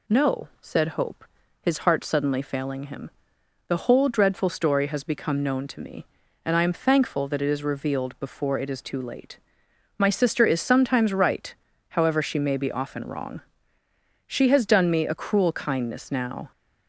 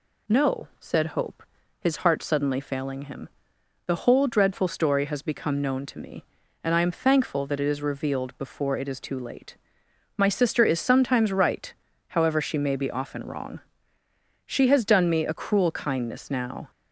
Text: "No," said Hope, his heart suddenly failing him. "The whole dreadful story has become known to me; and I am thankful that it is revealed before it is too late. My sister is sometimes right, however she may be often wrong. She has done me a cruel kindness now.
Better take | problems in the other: neither | none

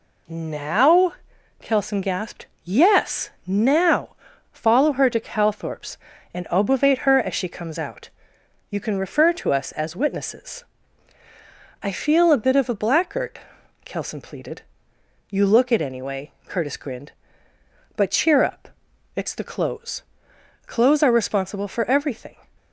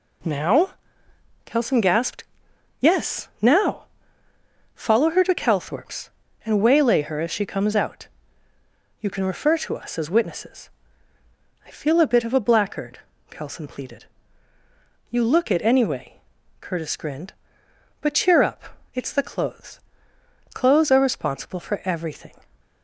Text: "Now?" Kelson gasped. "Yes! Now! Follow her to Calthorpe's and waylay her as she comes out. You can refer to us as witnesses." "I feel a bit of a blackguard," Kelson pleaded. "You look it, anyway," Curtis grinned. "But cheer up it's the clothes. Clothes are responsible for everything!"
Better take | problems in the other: second | says "obovate" for "waylay"; at 6.4 s // pauses between "up" and "it's"; noticeable; at 18.6 s; 0.46 s long; slight in the second

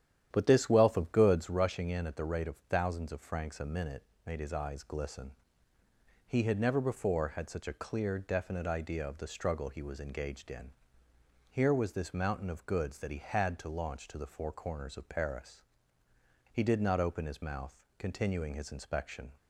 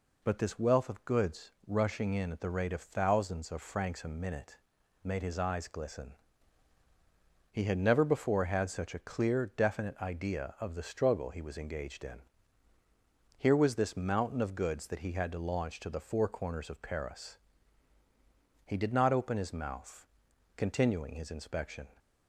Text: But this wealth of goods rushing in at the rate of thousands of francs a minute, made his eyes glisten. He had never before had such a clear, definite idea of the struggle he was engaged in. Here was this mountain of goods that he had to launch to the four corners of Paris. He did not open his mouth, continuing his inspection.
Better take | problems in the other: second | starts louder than the rest; strong; until 1.6 s; 10.5 dB

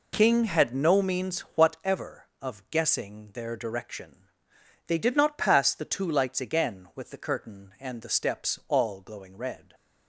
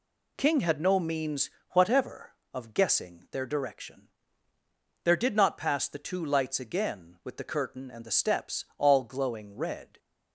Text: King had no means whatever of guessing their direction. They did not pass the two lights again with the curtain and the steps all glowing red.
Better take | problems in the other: first | pauses between "means" and "whatever"; slight; at 1.4 s; 0.22 s long; slight in the first // says "There" for "They"; at 5.0 s

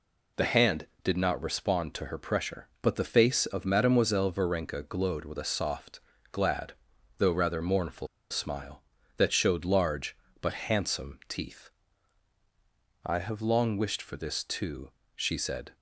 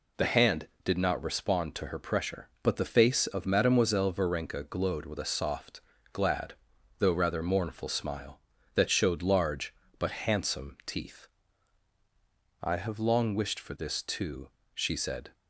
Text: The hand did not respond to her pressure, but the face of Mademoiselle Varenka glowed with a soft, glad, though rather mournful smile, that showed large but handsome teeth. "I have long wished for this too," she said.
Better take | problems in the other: second | pauses between "mournful" and "smile"; slight; at 8.0 s; 0.23 s long

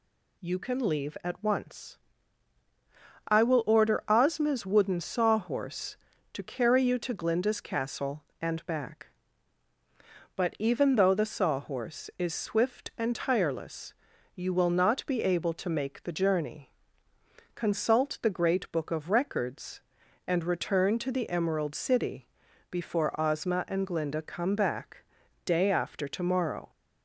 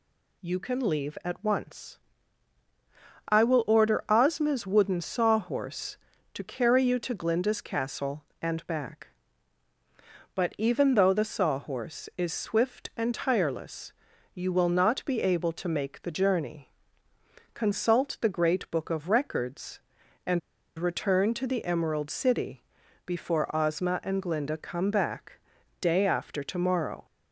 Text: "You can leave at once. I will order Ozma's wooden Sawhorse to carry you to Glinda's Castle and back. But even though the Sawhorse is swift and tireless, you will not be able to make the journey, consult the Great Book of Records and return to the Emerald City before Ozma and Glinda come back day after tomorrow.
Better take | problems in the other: first | pauses between "and" and "return"; at 20.3 s; 0.37 s long // pauses between "City" and "before"; at 22.6 s; 0.44 s long; also in the first // pauses between "back" and "day"; at 25.3 s; 0.40 s long; also in the first

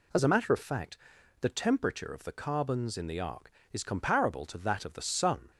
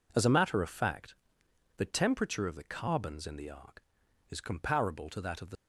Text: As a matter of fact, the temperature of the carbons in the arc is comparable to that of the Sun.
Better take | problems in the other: first | stops before "Sun"; at 5.5 s

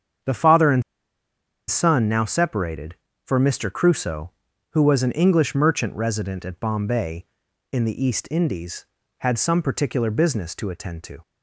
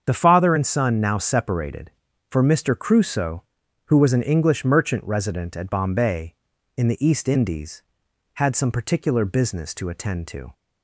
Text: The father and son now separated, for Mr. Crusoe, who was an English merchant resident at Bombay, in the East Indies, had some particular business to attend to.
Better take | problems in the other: second | starts louder than the rest; strong; until 2.1 s; 7.5 dB; also in the second // pauses between "and" and "son"; noticeable; at 0.8 s; 0.87 s long

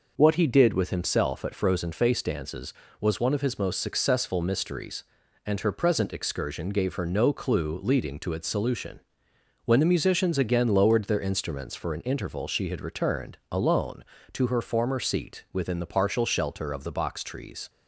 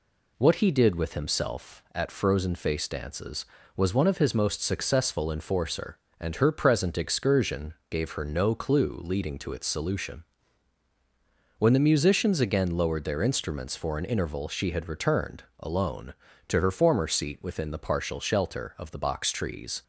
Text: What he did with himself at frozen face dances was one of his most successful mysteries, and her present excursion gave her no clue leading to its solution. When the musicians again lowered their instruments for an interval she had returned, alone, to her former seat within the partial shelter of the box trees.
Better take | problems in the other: first | says "enforcer" for "mysteries"; at 5.3 s // pauses between "excursion" and "gave"; slight; at 7.7 s; 0.16 s long

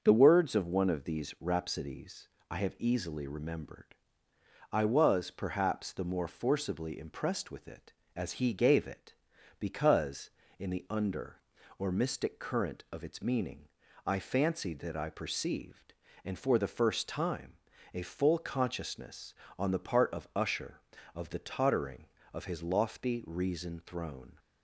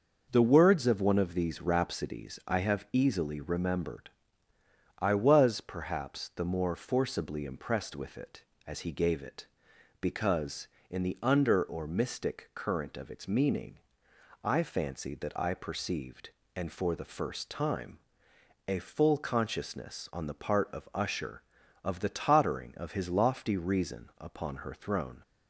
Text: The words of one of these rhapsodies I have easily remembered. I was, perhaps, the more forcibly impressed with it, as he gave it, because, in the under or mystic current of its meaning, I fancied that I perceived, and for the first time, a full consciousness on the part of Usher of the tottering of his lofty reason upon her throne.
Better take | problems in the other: second | starts louder than the rest; until 1.0 s; 6.5 dB // pauses between "rhapsodies" and "I"; slight; at 2.2 s; 0.20 s long // skips "upon her"; at 23.8 s

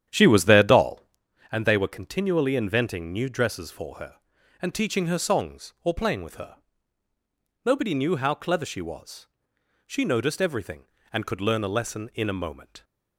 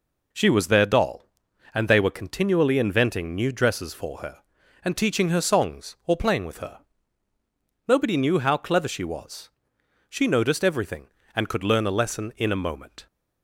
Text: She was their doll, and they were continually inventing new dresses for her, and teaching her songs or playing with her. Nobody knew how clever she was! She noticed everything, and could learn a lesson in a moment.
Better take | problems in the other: second | starts louder than the rest; strong; until 1.3 s; 10 dB

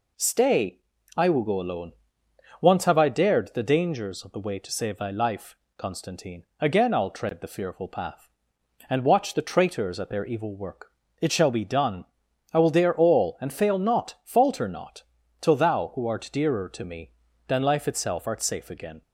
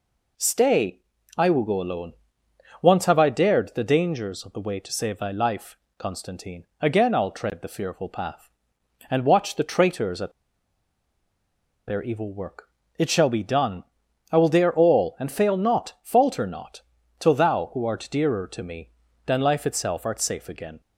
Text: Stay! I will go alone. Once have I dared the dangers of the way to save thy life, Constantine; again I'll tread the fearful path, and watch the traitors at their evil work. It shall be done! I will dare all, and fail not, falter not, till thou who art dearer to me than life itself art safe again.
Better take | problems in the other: first | pauses between "at" and "their"; strong; at 10.3 s; 1.5 s long

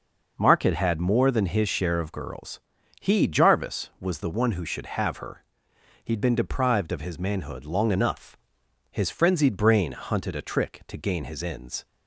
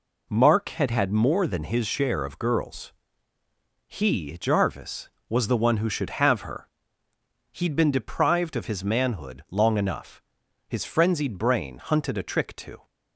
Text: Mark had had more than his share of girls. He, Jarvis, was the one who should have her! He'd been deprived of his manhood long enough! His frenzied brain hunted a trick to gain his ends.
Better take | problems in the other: first | stops before "gain his ends"; at 12.8 s

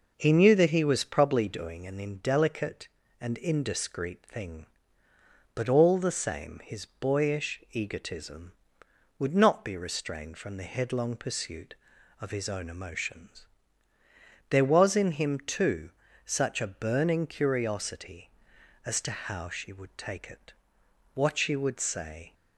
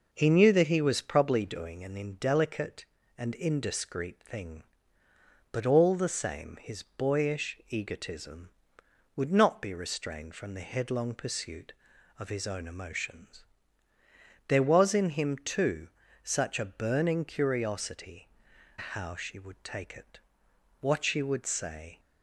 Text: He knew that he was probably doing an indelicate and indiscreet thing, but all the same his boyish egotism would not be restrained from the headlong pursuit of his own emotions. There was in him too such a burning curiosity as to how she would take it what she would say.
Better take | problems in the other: first | pauses between "too" and "such"; slight; at 15.8 s; 0.36 s long; slight in the first // skips "as to"; at 18.5 s // pauses between "it" and "what"; noticeable; at 20.1 s; 0.62 s long; noticeable in the first

